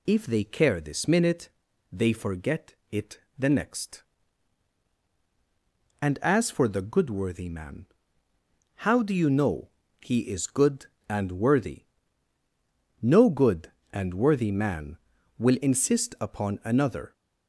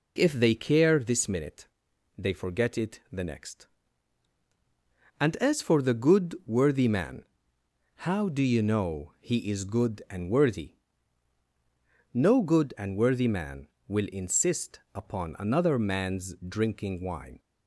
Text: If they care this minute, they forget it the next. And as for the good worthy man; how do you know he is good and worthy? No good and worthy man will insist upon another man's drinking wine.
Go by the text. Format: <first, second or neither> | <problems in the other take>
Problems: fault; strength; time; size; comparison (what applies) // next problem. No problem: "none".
second | pauses between "forget" and "it"; slight; at 2.7 s; 0.18 s long // pauses between "it" and "the"; slight; at 3.1 s; 0.20 s long // pauses between "know" and "he"; slight; at 9.6 s; 0.32 s long // stops before "man's drinking wine"; at 17.1 s